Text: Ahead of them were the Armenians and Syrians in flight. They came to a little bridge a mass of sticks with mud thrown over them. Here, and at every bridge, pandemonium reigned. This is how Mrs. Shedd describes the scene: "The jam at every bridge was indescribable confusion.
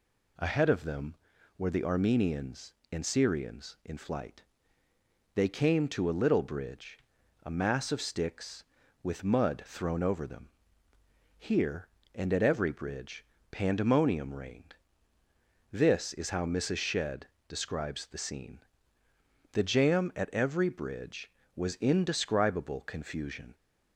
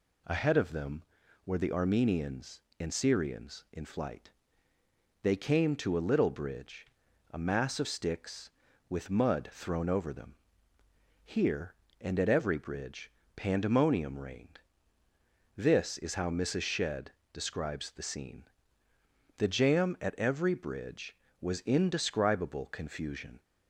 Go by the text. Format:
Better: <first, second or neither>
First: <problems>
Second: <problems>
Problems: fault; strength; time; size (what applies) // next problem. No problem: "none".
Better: neither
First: pauses between "bridge" and "a"; noticeable; at 6.9 s; 0.48 s long // pauses between "Shedd" and "describes"; slight; at 17.2 s; 0.20 s long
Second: pauses between "bridge" and "a"; noticeable; at 6.8 s; 0.48 s long // pauses between "Shedd" and "describes"; slight; at 17.1 s; 0.20 s long